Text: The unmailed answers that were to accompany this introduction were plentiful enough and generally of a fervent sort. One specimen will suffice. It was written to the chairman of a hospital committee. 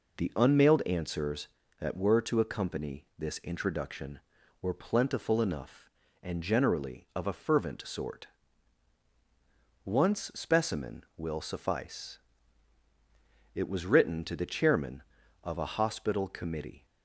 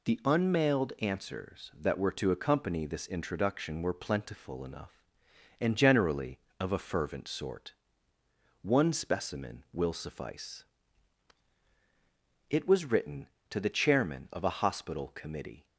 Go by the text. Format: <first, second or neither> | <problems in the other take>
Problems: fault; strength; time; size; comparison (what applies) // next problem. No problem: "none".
second | says "Once" for "One"; at 9.8 s